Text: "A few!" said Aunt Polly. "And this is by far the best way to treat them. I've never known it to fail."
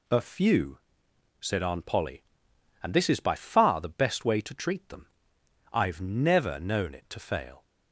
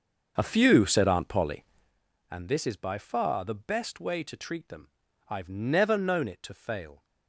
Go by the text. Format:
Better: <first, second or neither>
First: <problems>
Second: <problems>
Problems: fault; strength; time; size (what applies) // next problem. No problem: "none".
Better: first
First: none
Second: starts louder than the rest; until 2.0 s; 6.5 dB